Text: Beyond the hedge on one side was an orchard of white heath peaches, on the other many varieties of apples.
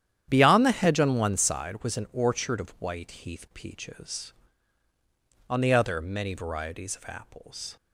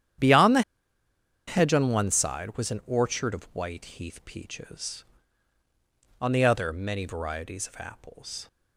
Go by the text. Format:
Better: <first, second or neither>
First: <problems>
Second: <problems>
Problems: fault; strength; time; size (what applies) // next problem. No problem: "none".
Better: first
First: starts louder than the rest; strong; until 1.3 s; 10 dB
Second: starts louder than the rest; strong; until 2.0 s; 10 dB // pauses between "the" and "hedge"; noticeable; at 0.6 s; 0.86 s long